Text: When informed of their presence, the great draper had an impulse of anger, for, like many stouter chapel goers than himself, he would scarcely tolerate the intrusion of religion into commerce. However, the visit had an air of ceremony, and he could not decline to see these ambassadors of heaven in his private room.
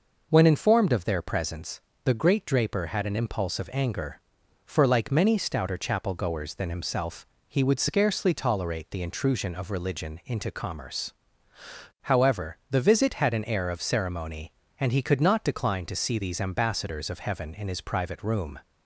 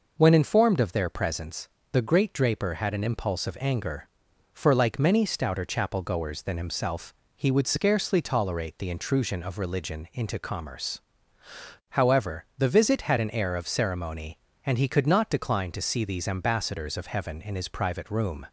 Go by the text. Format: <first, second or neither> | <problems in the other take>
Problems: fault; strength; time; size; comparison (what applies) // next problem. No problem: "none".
neither | none